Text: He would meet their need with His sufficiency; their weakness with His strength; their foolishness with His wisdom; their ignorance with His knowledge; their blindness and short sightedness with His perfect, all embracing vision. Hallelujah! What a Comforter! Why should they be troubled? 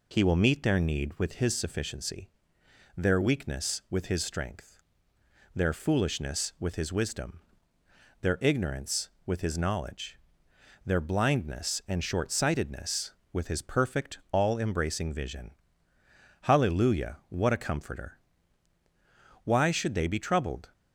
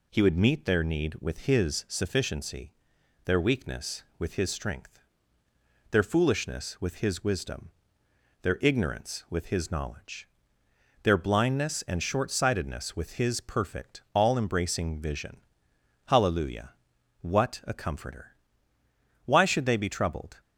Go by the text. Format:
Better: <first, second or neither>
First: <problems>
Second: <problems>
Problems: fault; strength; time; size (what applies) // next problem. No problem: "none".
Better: second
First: says "will" for "would"; at 0.2 s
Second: none